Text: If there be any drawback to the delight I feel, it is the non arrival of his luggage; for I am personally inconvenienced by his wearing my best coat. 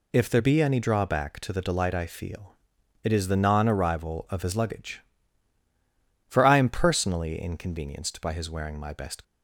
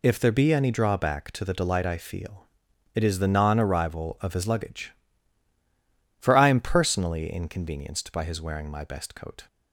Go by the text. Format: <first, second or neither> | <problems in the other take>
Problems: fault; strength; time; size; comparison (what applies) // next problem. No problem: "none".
second | stops before "coat"; at 9.2 s